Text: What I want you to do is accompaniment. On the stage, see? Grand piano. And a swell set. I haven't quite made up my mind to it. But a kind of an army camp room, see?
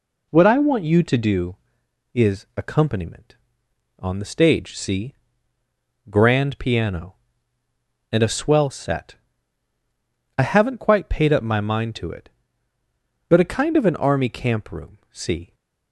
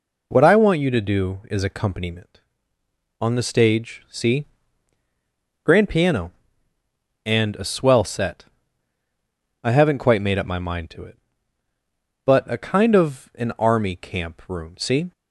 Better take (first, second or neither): second